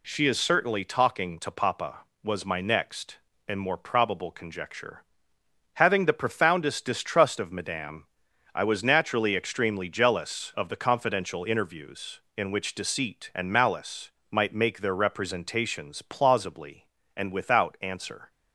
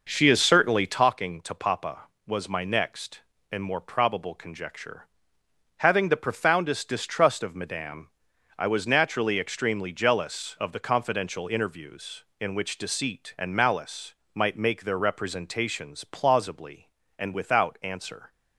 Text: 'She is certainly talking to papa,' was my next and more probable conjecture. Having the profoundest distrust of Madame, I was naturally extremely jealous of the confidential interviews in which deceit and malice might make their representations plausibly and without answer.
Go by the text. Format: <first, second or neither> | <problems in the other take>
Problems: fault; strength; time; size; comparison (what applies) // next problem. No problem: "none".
first | starts louder than the rest; noticeable; until 1.1 s; 5.5 dB // pauses between "malice" and "might"; slight; at 14.1 s; 0.20 s long; slight in the first